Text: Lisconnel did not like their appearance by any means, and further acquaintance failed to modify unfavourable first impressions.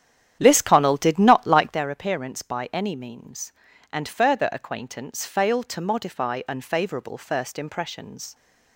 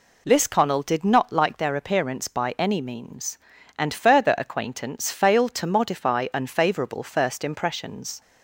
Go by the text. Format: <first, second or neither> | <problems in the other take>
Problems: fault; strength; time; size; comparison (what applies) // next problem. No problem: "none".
second | starts louder than the rest; strong; until 1.9 s; 10 dB